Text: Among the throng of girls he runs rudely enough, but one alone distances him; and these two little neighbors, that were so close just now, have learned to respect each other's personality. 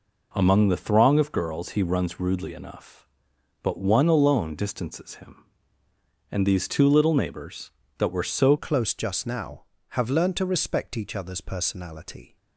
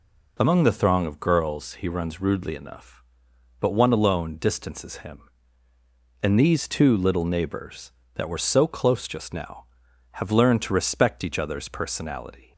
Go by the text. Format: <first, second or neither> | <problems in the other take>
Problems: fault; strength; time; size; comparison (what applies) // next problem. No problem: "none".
second | changes voice at "close"; from 8.5 s on; 3.8 s long